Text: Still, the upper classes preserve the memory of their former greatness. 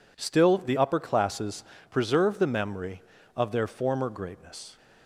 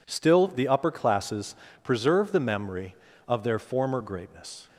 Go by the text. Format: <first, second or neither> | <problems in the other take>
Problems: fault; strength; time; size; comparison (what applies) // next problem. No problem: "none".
neither | pauses between "classes" and "preserve"; slight; the same in both